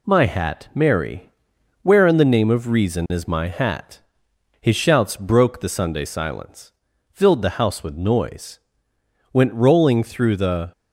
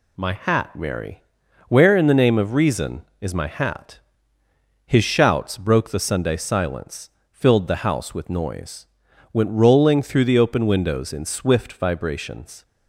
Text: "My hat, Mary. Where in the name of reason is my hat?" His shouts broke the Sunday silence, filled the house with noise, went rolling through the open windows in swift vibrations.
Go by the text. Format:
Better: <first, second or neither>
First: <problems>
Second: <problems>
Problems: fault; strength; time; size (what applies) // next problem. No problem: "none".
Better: second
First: stops before "open windows in swift vibrations"; at 10.7 s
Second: none